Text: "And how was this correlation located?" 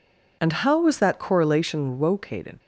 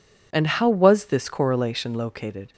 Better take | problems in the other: second | says "that" for "this"; at 0.9 s

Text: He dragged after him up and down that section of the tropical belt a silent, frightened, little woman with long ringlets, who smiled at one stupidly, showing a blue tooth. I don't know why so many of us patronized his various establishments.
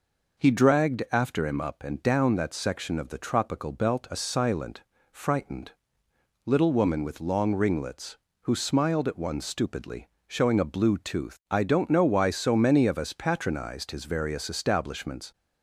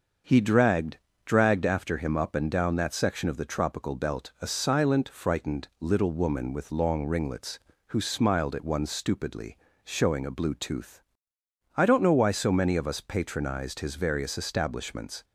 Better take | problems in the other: first | starts louder than the rest; until 1.5 s; 6.5 dB // says "dragged" twice; at 1.2 s

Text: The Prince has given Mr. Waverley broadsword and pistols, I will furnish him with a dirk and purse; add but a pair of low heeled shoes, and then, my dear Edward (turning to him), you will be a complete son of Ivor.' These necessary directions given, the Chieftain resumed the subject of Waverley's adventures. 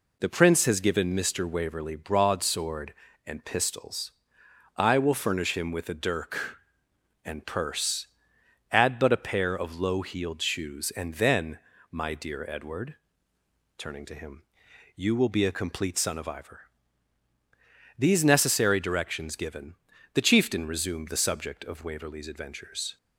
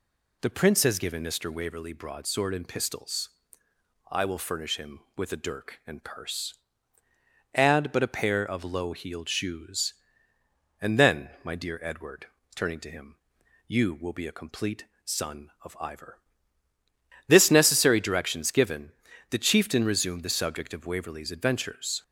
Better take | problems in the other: first | pauses between "complete" and "son"; slight; at 14.8 s; 0.22 s long // says "This" for "These"; at 17.2 s

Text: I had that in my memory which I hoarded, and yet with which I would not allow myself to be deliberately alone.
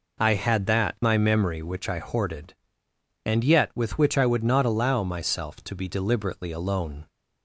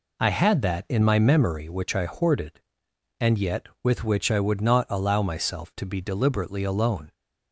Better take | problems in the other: second | skips "in"; at 0.9 s

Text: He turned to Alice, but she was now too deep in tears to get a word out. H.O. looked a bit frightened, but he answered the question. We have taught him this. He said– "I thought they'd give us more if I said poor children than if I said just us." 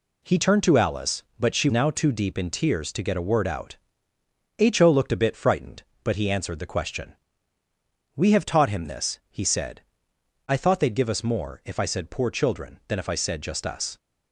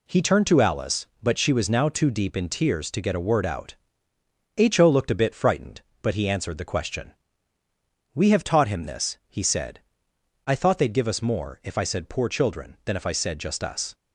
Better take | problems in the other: second | skips "was"; at 1.6 s

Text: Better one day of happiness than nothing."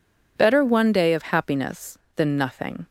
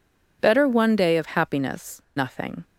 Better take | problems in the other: first | skips "than"; at 2.0 s

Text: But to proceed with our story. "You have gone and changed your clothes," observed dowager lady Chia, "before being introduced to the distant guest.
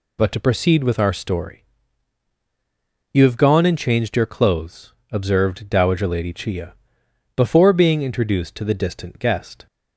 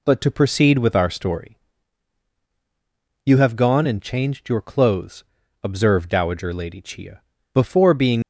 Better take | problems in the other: first | stops before "introduced to the distant guest"; at 8.2 s

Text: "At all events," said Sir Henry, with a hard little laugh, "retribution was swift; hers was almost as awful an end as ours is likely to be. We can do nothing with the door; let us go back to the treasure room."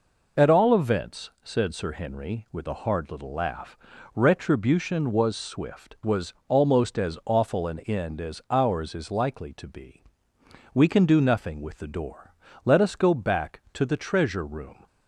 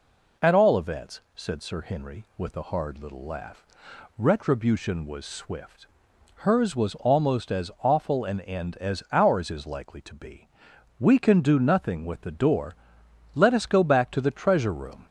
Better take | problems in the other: second | skips "hers"; at 5.9 s

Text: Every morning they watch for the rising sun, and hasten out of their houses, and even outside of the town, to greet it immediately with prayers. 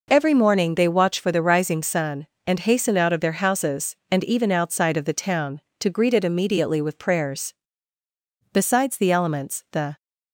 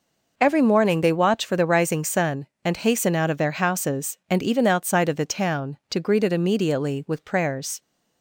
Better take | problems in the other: second | goes on to say "Besides the elements the"; from 8.5 s on; 1.4 s long

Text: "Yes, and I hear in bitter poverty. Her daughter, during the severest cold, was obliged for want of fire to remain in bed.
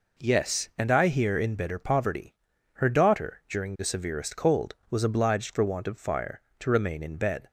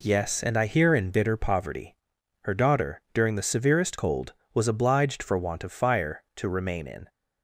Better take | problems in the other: first | stops before "bed"; at 7.0 s

